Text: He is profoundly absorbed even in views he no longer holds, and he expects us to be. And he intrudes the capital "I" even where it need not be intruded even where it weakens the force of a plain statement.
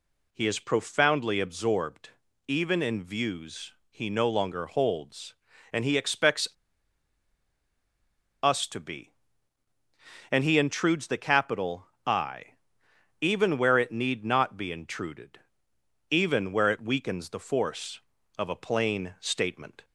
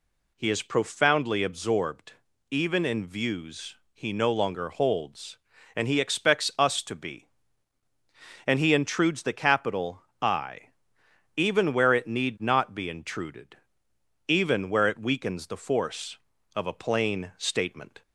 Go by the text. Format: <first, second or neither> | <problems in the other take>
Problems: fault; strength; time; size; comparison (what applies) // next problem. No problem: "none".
second | pauses between "absorbed" and "even"; slight; at 2.1 s; 0.36 s long; slight in the second // pauses between "views" and "he"; slight; at 3.7 s; 0.18 s long; slight in the second // pauses between "expects" and "us"; strong; at 6.4 s; 1.9 s long // pauses between "capital" and "I"; slight; at 11.8 s; 0.20 s long; slight in the second // pauses between "I" and "even"; noticeable; at 12.5 s; 0.66 s long; noticeable in the second // pauses between "intruded" and "even"; noticeable; at 15.3 s; 0.72 s long; noticeable in the second